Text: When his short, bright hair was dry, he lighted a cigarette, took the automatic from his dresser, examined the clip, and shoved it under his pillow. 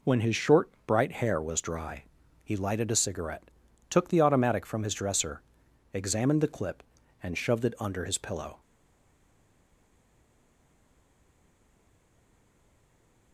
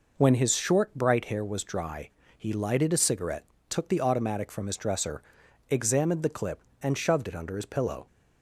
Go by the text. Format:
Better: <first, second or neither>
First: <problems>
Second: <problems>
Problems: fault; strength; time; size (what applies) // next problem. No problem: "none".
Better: second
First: stays silent after the last word; strong; from 8.6 s on; 4.7 s long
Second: none